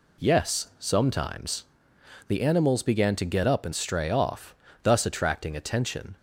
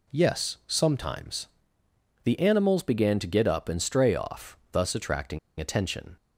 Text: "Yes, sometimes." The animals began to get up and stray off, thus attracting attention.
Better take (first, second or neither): first